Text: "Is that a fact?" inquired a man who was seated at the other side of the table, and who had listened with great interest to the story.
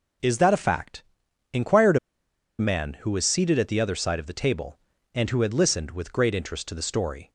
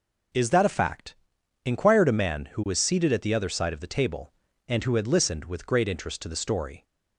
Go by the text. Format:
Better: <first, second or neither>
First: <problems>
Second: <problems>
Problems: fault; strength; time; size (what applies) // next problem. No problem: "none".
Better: second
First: pauses between "inquired" and "a"; noticeable; at 1.9 s; 0.62 s long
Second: none